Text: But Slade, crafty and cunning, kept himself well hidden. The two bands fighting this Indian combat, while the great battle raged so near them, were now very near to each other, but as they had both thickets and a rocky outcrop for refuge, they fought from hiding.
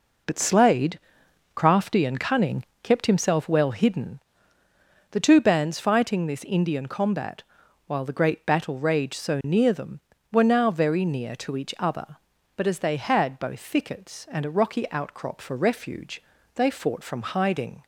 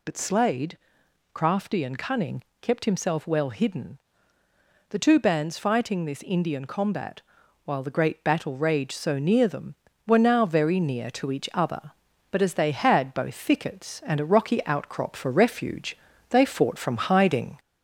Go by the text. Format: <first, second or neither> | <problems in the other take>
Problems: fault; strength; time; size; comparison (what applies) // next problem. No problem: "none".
first | gets louder; slight; throughout; 3 dB